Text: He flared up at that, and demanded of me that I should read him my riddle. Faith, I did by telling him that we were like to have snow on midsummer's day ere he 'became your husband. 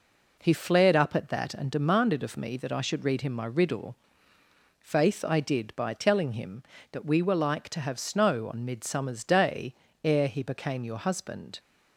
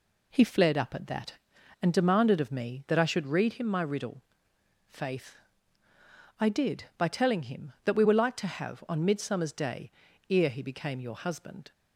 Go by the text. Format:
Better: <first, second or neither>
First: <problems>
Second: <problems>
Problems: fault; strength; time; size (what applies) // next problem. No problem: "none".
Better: first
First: pauses between "day" and "ere"; slight; at 9.7 s; 0.30 s long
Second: skips "snow"; at 8.8 s // pauses between "day" and "ere"; at 9.9 s; 0.38 s long